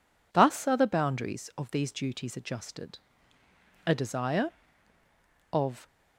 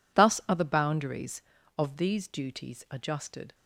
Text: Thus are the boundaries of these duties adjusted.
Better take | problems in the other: second | goes on to say "A desire of"; strong; from 3.8 s on; 2.0 s long

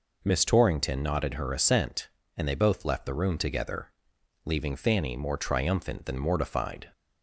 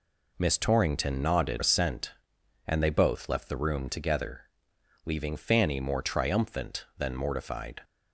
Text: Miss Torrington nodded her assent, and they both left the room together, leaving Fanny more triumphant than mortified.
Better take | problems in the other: first | skips "her"; at 1.6 s

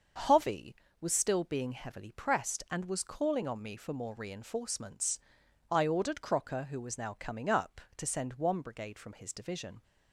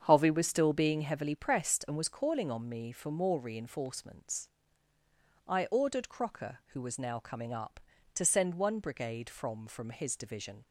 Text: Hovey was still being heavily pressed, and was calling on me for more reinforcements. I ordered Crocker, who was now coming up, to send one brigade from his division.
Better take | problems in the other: first | starts louder than the rest; strong; until 1.0 s; 7.5 dB; also in the first // says "from" twice; at 9.6 s

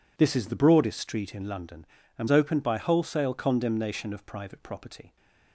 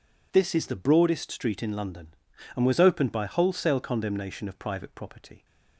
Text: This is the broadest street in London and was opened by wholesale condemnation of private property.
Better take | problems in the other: second | skips "was"; at 2.2 s

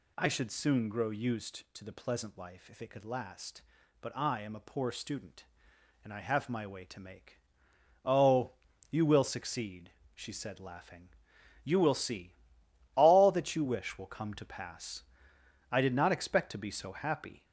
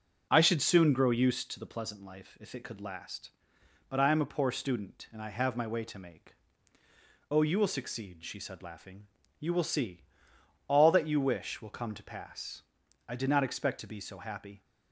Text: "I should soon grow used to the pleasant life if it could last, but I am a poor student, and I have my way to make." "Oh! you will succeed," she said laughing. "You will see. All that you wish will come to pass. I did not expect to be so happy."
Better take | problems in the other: second | gets louder; noticeable; throughout; 4.5 dB

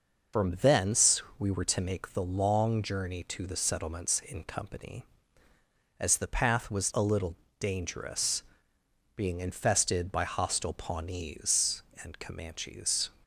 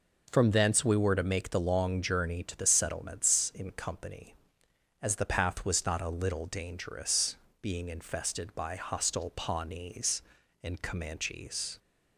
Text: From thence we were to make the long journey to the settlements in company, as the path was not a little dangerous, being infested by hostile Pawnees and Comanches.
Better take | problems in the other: second | pauses between "thence" and "we"; slight; at 1.2 s; 0.16 s long // skips "not"; at 6.9 s // pauses between "little" and "dangerous"; slight; at 7.3 s; 0.24 s long

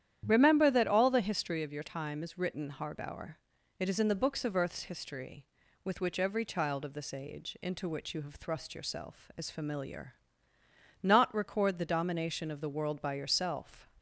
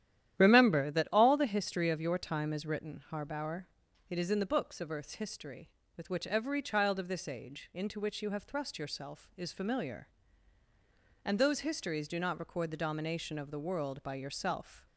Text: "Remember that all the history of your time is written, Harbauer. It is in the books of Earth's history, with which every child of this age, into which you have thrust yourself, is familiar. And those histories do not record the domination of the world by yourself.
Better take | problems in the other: second | starts louder than the rest; strong; until 1.2 s; 10.5 dB; strong in the second // skips "And those histories do"; at 10.5 s

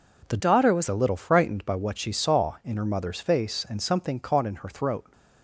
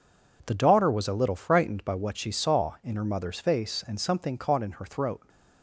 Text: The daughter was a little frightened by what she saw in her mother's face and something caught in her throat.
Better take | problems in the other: second | changes voice from "daughter" to "was"; from 0.3 to 0.8 s; 0.5 s long

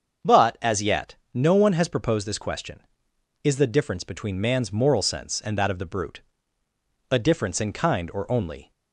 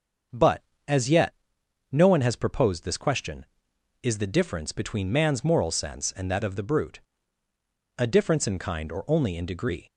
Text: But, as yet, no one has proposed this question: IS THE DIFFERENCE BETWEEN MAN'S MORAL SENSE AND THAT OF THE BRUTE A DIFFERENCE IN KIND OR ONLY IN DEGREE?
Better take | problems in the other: second | starts louder than the rest; until 1.4 s; 7 dB; also in the second // pauses between "BRUTE" and "A"; noticeable; at 6.2 s; 0.90 s long; noticeable in the second // stops before "IN DEGREE"; at 8.7 s

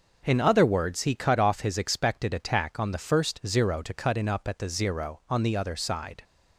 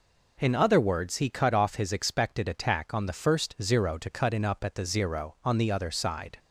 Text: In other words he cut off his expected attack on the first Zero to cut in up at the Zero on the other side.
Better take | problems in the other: second | gets quieter; throughout; 6.5 dB

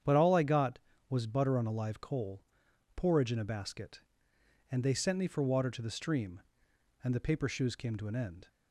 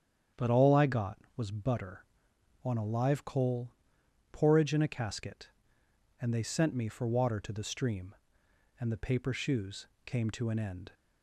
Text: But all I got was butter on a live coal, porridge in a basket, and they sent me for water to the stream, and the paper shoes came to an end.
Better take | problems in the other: first | starts louder than the rest; strong; until 1.5 s; 8.5 dB; strong in the first // says "casket" for "basket"; at 4.8 s // pauses between "shoes" and "came"; slight; at 9.8 s; 0.20 s long

